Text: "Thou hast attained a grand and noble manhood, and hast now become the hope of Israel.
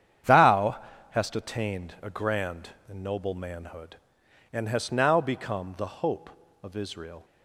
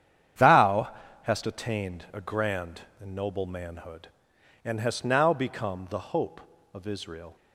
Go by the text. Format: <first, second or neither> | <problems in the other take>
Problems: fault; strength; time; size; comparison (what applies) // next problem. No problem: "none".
neither | starts louder than the rest; strong; the same in both // pauses between "Thou" and "hast"; slight; the same in both